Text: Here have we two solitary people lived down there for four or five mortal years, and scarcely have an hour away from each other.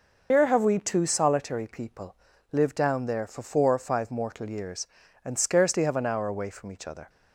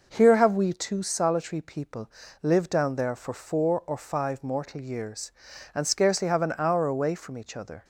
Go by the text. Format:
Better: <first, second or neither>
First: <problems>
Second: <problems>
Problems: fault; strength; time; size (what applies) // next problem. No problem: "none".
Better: second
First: loses the start of "Here"; at 0.3 s; 115 ms // pauses between "people" and "lived"; slight; at 2.1 s; 0.36 s long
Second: pauses between "people" and "lived"; slight; at 2.0 s; 0.32 s long